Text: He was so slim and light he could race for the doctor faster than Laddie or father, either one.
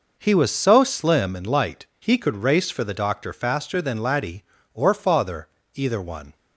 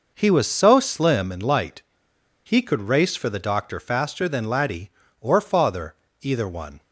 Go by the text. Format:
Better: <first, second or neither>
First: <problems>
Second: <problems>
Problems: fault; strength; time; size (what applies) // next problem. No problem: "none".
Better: first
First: none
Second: pauses between "light" and "he"; noticeable; at 1.8 s; 0.62 s long